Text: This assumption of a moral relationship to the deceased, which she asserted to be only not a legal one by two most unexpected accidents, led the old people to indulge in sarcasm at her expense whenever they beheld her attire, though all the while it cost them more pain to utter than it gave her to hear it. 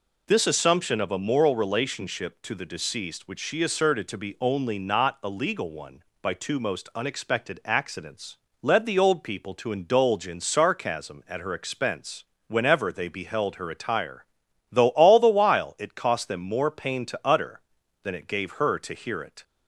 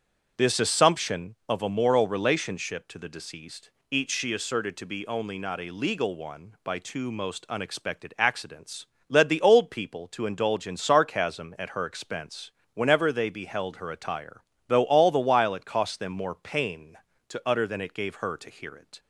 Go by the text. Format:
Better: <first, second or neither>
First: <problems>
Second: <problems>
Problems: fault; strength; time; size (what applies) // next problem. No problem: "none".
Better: first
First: pauses between "expense" and "whenever"; slight; at 12.2 s; 0.24 s long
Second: starts louder than the rest; strong; until 1.5 s; 7.5 dB // says "each" for "which"; at 3.8 s // pauses between "expense" and "whenever"; slight; at 12.5 s; 0.22 s long